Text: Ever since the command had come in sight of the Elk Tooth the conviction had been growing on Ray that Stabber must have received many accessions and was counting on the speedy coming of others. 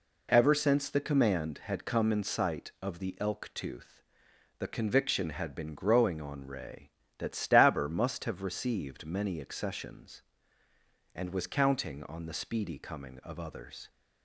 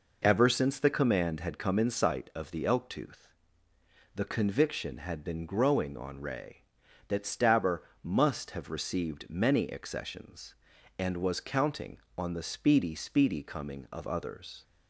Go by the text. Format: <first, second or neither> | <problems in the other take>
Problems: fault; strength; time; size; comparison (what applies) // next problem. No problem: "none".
first | pauses between "Tooth" and "the"; noticeable; at 3.2 s; 0.88 s long; noticeable in the first // pauses between "Stabber" and "must"; slight; at 7.8 s; 0.20 s long // says "speedy" twice; at 12.9 s